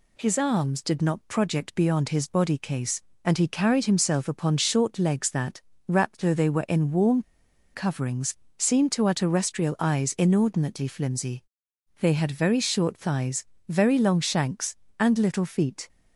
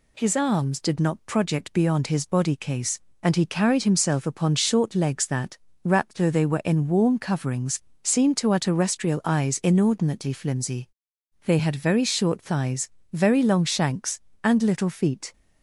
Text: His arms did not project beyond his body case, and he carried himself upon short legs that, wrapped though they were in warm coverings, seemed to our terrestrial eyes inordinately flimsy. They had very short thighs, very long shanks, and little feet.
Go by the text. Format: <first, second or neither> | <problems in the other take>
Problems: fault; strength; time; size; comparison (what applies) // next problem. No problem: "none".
second | pauses between "warm" and "coverings"; noticeable; at 7.2 s; 0.53 s long